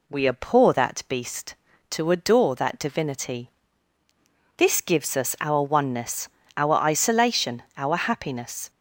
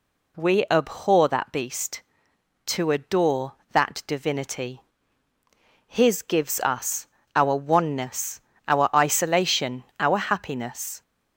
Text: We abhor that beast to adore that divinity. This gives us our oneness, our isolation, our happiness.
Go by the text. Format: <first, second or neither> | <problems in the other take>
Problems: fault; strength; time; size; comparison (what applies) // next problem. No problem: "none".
first | says "His" for "This"; at 5.8 s // pauses between "us" and "our"; slight; at 7.0 s; 0.26 s long